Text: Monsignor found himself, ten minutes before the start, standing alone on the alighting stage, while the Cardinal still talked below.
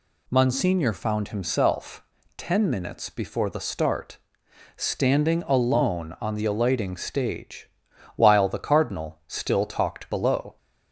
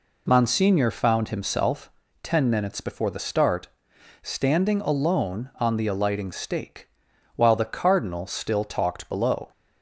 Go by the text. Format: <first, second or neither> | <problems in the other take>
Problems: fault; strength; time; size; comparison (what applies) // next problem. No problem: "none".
first | says "stake" for "stage"; at 6.3 s